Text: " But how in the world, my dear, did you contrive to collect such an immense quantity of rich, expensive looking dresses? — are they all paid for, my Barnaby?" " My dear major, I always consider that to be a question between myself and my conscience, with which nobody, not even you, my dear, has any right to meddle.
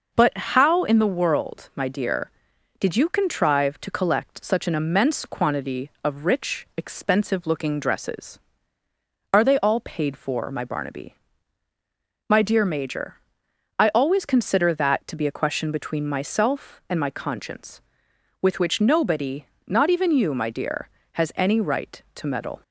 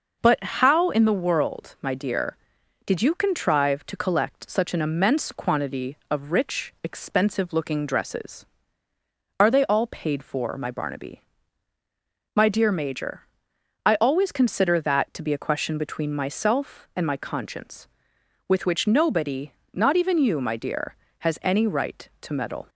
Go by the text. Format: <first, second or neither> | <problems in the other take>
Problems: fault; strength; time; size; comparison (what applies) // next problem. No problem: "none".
neither | pauses between "But" and "how"; slight; the same in both